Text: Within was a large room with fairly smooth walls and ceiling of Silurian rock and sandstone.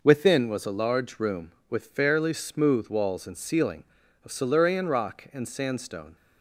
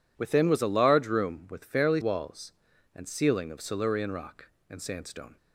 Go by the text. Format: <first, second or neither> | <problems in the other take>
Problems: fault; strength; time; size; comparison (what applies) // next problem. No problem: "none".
first | skips "smooth"; at 2.0 s